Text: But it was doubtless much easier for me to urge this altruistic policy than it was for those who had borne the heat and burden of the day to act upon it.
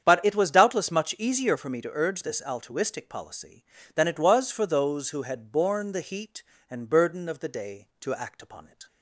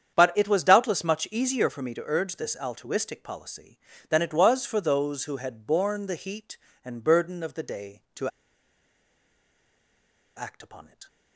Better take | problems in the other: first | starts louder than the rest; strong; until 1.1 s; 8.5 dB; strong in the first // pauses between "to" and "act"; strong; at 8.2 s; 2.0 s long

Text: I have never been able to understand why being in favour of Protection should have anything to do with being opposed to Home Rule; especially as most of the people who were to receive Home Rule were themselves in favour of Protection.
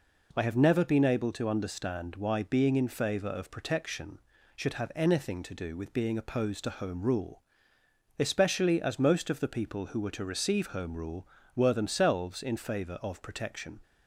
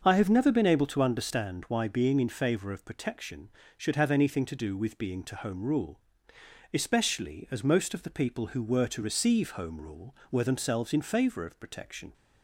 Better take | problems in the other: first | starts louder than the rest; until 1.0 s; 6.5 dB // skips "opposed"; at 5.2 s

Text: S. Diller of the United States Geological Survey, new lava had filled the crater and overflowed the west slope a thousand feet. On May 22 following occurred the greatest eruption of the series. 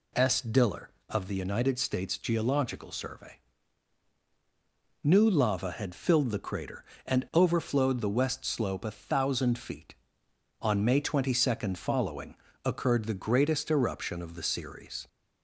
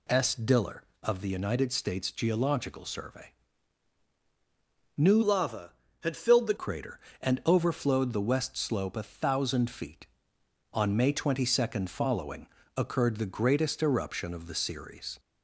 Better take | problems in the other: first | changes voice from "lava" to "the"; from 5.2 to 6.5 s; 1.3 s long // pauses between "following" and "occurred"; slight; at 12.4 s; 0.30 s long; slight in the first

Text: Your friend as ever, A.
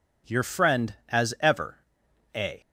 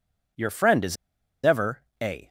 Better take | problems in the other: first | pauses between "as" and "ever"; noticeable; at 0.9 s; 0.48 s long

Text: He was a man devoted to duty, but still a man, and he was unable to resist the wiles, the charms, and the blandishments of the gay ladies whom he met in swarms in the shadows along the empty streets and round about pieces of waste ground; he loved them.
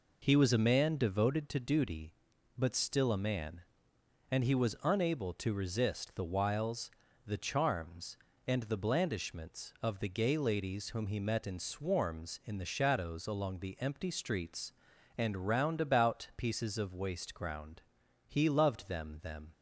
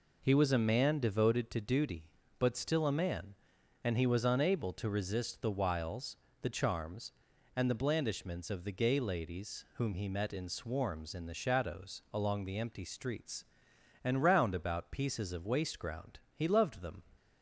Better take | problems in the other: second | says "them" twice; at 19.2 s

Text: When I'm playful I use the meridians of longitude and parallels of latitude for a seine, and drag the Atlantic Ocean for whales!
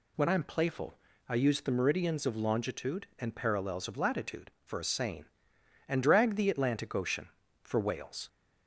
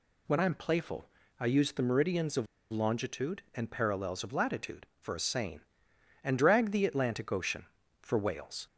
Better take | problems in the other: first | pauses between "playful" and "I"; slight; at 1.0 s; 0.32 s long; slight in the first // pauses between "of" and "longitude"; slight; at 2.4 s; 0.25 s long

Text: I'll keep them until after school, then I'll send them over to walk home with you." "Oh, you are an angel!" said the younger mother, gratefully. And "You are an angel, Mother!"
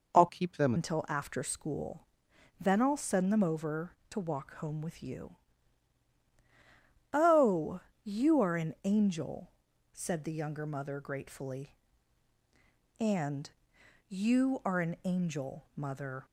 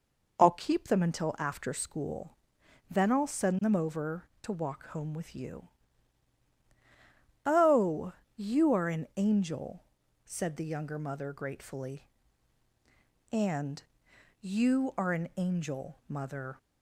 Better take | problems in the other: second | changes voice from "keep" to "them"; from 0.2 to 0.7 s; 0.5 s long // pauses between "And" and "You"; noticeable; at 13.4 s; 0.60 s long; noticeable in the second

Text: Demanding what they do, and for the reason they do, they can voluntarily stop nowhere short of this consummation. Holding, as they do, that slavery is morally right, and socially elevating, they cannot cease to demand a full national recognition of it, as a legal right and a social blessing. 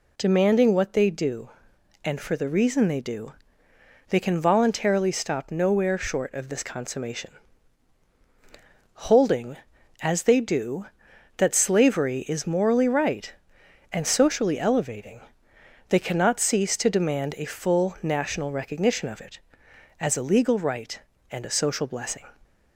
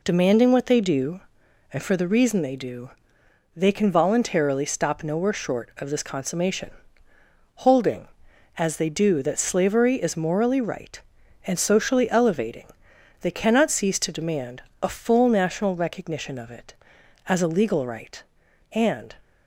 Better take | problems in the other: first | pauses between "demand" and "a"; slight; at 14.6 s; 0.20 s long // stops before "a social blessing"; at 19.2 s

